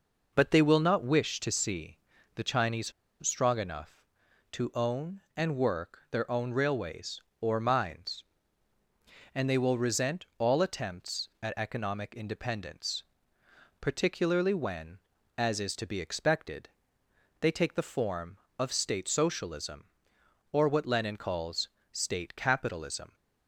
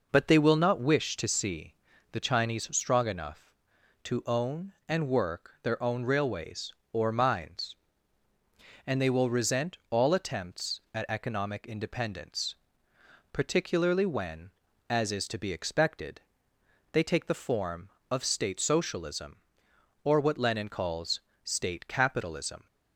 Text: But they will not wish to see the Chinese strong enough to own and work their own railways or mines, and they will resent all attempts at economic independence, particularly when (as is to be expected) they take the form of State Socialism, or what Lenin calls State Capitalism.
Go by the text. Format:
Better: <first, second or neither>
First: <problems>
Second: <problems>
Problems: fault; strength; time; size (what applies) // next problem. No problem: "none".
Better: second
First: pauses between "see" and "the"; at 1.9 s; 0.38 s long // pauses between "Chinese" and "strong"; slight; at 2.9 s; 0.35 s long // pauses between "calls" and "State"; slight; at 21.6 s; 0.22 s long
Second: pauses between "see" and "the"; at 1.7 s; 0.38 s long // pauses between "calls" and "State"; slight; at 21.2 s; 0.22 s long